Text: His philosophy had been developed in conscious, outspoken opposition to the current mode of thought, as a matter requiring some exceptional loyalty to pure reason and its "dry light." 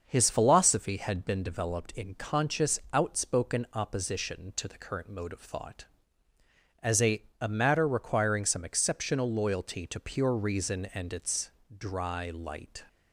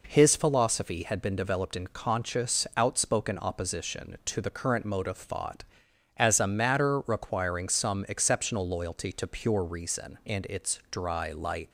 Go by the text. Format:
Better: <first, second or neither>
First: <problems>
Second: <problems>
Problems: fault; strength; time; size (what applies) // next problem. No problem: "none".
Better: second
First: starts louder than the rest; until 1.0 s; 6.5 dB // says "a" twice; at 7.4 s // pauses between "its" and "dry"; slight; at 11.5 s; 0.28 s long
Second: none